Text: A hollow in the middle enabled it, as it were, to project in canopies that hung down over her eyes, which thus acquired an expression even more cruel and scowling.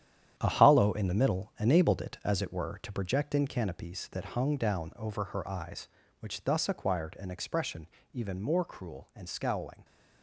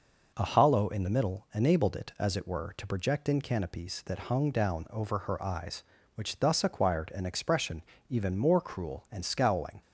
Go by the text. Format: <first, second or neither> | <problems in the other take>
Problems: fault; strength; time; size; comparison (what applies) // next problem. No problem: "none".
second | gets quieter; strong; throughout; 9 dB // pauses between "expression" and "even"; slight; at 7.8 s; 0.25 s long; slight in the second